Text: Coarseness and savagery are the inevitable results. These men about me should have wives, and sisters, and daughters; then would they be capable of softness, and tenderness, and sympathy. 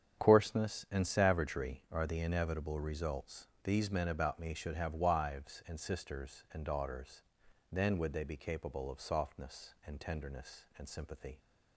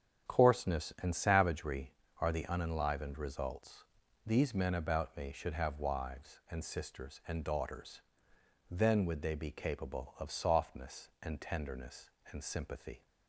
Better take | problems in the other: first | starts louder than the rest; strong; until 1.3 s; 8.5 dB; strong in the first // says "unenlivened" for "inevitable"; at 2.4 s

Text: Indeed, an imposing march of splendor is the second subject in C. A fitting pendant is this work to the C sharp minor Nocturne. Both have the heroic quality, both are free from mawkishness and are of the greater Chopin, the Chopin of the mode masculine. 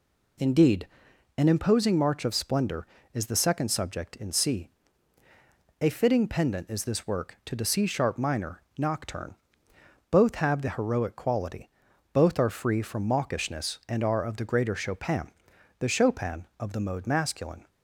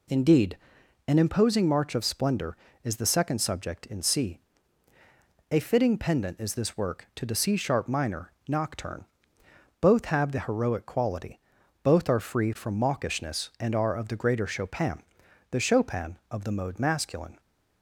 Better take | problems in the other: neither | pauses between "minor" and "Nocturne"; slight; the same in both

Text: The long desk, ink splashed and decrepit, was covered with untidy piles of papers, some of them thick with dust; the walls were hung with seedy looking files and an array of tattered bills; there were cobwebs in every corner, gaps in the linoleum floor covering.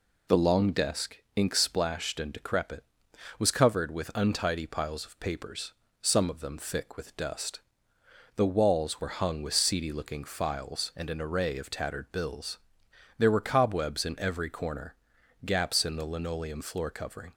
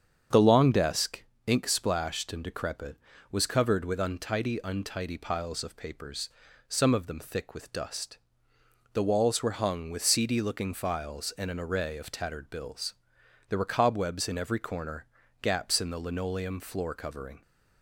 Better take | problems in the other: first | starts louder than the rest; strong; until 1.5 s; 7.5 dB // says "untidy" twice; at 4.6 s

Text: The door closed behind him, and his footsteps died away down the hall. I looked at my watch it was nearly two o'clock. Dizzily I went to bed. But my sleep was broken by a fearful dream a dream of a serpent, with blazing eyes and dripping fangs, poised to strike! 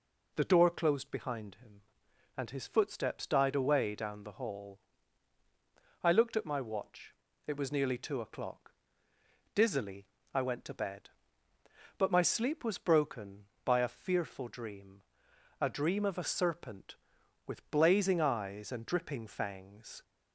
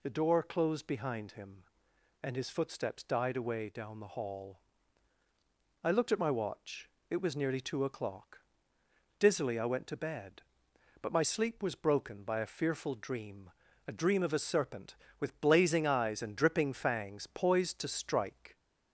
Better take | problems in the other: second | pauses between "watch" and "it"; slight; at 7.1 s; 0.32 s long; slight in the second // pauses between "Dizzily" and "I"; slight; at 10.0 s; 0.28 s long // pauses between "dream" and "a"; noticeable; at 15.0 s; 0.58 s long; also in the second // stops before "poised to strike"; at 20.0 s

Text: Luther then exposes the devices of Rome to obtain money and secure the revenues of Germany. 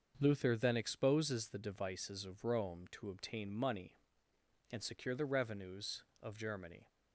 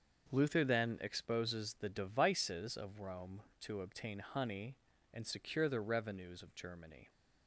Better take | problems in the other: first | starts louder than the rest; until 1.3 s; 6.5 dB; also in the first // says "honey" for "money"; at 4.1 s

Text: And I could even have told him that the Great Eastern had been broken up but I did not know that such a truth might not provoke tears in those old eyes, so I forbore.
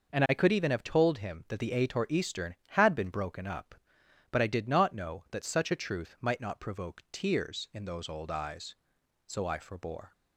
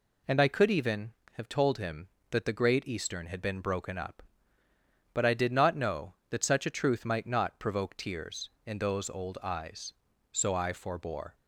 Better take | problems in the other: second | says "Ator" for "Great"; at 1.7 s

